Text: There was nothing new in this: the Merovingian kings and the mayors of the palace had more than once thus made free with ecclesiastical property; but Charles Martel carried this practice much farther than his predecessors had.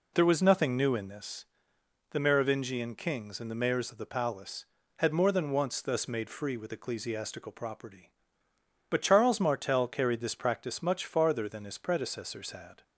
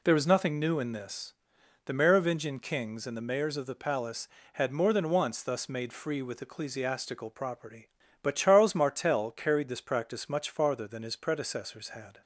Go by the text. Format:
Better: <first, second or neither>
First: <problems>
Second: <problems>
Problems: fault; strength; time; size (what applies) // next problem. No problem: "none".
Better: neither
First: none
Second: none